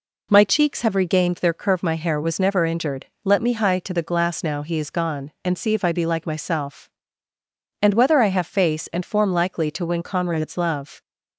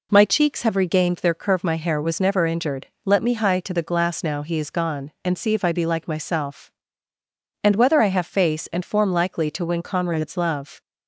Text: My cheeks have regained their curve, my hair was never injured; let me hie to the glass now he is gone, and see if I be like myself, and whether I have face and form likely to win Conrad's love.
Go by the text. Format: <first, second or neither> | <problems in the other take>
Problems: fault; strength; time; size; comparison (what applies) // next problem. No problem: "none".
neither | none